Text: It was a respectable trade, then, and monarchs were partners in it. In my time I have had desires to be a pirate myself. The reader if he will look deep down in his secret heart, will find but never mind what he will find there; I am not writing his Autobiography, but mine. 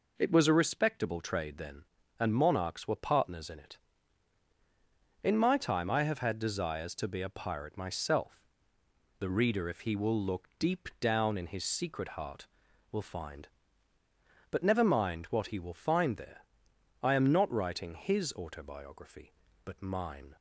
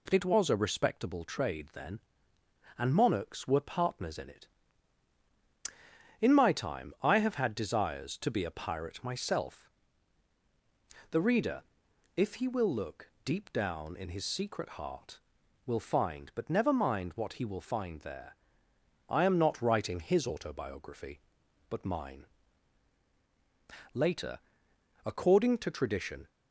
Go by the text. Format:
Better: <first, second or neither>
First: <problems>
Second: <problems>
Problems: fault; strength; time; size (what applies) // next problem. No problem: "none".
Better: first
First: none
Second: pauses between "reader" and "if"; noticeable; at 11.6 s; 0.52 s long // goes on to say "Later according to tradition"; strong; from 23.9 s on; 2.3 s long